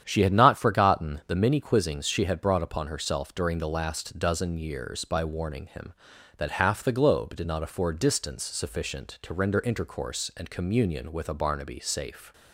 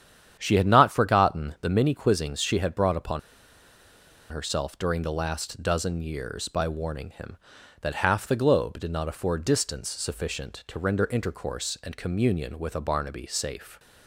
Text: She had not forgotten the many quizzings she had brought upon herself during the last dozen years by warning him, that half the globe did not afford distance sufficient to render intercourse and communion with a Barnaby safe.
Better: first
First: starts louder than the rest; strong; until 1.0 s; 9 dB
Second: starts louder than the rest; strong; until 1.4 s; 9 dB // pauses between "upon" and "herself"; at 3.1 s; 1.1 s long

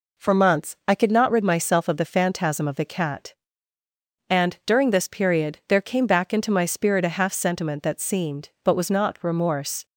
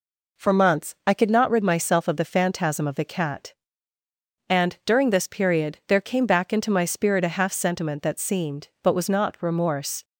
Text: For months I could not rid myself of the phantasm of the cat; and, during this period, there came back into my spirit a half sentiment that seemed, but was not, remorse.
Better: neither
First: none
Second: none

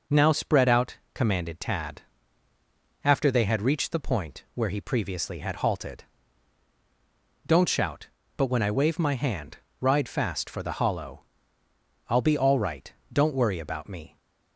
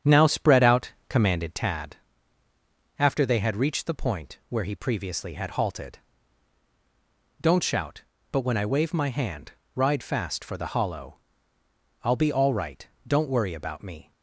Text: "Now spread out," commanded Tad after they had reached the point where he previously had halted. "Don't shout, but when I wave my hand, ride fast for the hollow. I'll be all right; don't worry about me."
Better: first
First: pauses between "Tad" and "after"; at 2.0 s; 1.0 s long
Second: starts louder than the rest; strong; until 1.9 s; 8.5 dB // pauses between "Tad" and "after"; at 1.9 s; 1.0 s long

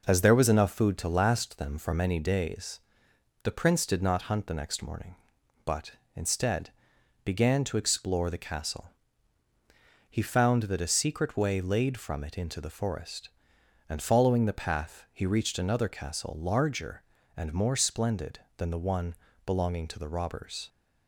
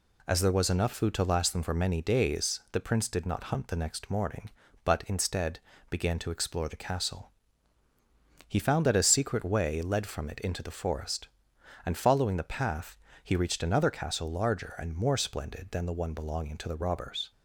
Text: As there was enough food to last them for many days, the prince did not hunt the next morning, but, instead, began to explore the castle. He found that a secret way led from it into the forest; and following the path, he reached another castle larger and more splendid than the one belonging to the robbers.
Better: second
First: says "laid" for "led"; at 11.6 s // pauses between "one" and "belonging"; slight; at 19.1 s; 0.32 s long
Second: none

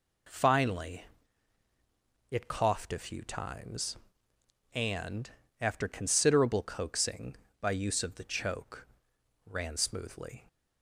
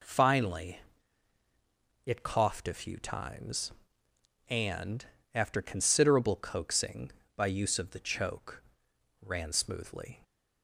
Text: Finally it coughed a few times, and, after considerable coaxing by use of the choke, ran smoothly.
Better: neither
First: pauses between "Finally" and "it"; at 1.0 s; 1.2 s long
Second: pauses between "Finally" and "it"; at 0.8 s; 1.2 s long

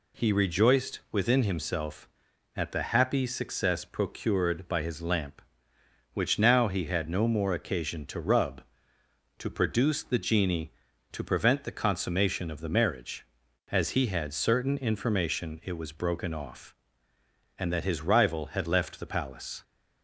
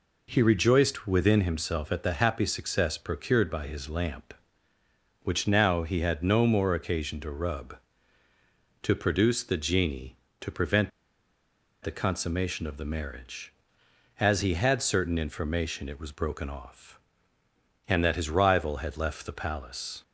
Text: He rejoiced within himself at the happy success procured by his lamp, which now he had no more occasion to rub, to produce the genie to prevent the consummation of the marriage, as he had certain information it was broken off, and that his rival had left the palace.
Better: first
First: none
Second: pauses between "prevent" and "the"; noticeable; at 10.9 s; 0.92 s long

